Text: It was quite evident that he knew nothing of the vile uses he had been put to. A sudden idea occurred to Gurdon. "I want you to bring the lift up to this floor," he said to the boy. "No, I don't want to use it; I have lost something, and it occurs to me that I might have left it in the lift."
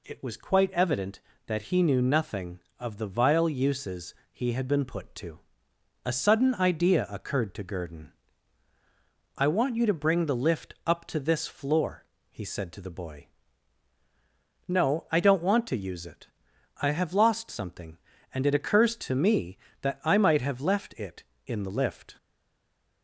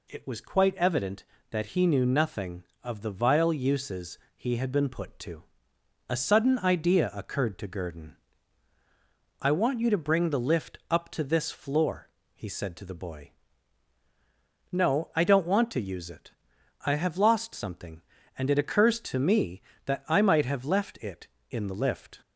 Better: second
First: pauses between "uses" and "he"; slight; at 4.1 s; 0.18 s long // stays silent after the last word; slight; from 22.1 s on; 0.9 s long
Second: pauses between "uses" and "he"; slight; at 4.1 s; 0.18 s long

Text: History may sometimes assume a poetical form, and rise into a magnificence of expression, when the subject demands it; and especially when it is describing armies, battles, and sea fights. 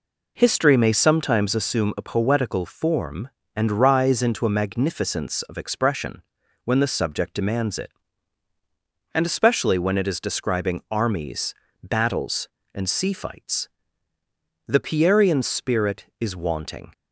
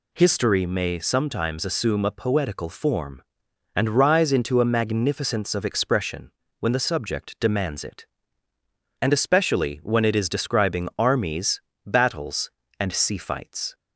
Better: second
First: goes on to say "The Pierian spirit is wanting"; strong; from 14.6 s on; 2.2 s long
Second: none

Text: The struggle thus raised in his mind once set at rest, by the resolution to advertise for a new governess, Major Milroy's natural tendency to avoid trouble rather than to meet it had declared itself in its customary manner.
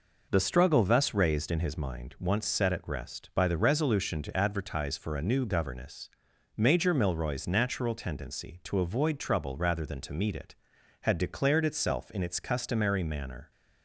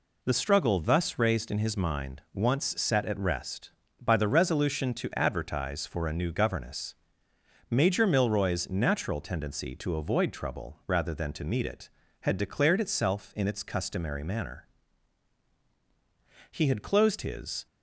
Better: first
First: none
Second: goes on to say "He had closed his"; noticeable; from 16.5 s on; 1.1 s long

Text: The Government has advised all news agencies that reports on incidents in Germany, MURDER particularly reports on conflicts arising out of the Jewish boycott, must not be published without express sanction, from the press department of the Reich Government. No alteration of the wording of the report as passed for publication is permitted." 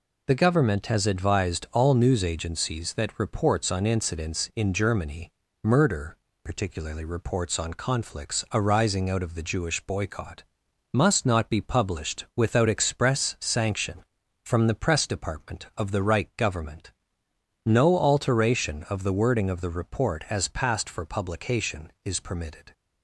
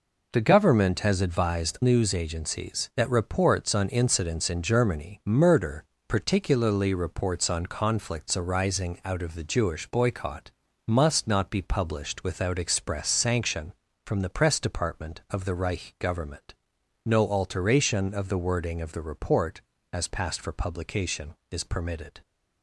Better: first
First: pauses between "MURDER" and "particularly"; slight; at 6.1 s; 0.28 s long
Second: skips "all"; at 1.7 s // pauses between "MURDER" and "particularly"; slight; at 5.8 s; 0.22 s long

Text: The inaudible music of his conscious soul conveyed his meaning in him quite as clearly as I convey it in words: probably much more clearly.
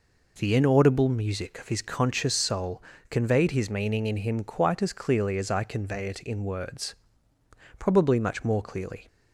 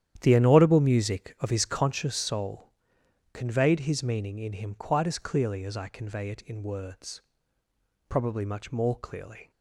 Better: first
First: pauses between "soul" and "conveyed"; slight; at 2.8 s; 0.26 s long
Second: starts louder than the rest; strong; until 2.0 s; 10.5 dB // pauses between "soul" and "conveyed"; noticeable; at 2.7 s; 0.62 s long

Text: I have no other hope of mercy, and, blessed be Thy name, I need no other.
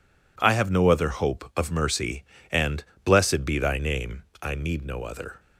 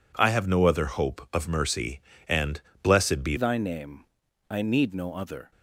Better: first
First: none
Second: changes voice at "Thy"; from 3.3 s on; 2.2 s long

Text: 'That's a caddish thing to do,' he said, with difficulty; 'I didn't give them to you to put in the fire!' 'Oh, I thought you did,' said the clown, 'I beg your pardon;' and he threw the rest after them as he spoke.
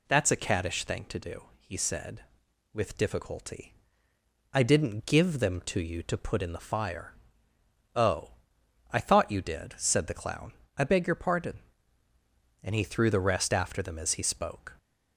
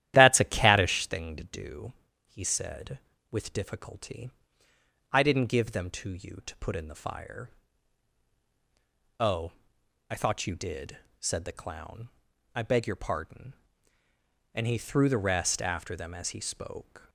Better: first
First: none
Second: starts louder than the rest; strong; until 1.1 s; 12.5 dB

